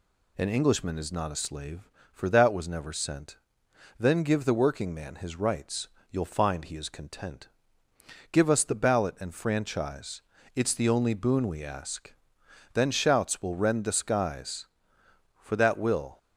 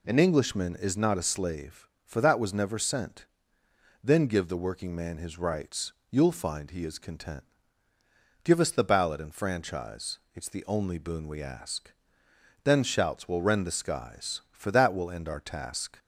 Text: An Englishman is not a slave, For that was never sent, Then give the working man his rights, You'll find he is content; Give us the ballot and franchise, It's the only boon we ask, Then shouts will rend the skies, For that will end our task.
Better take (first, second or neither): second